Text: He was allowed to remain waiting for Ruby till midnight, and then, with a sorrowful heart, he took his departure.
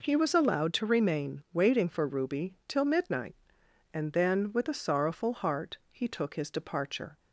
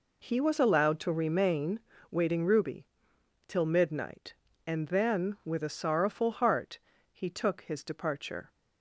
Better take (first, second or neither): first